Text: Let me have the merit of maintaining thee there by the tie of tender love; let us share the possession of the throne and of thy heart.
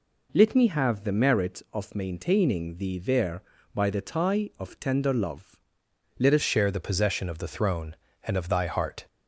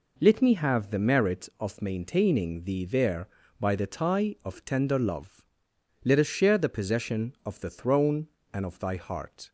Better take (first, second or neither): second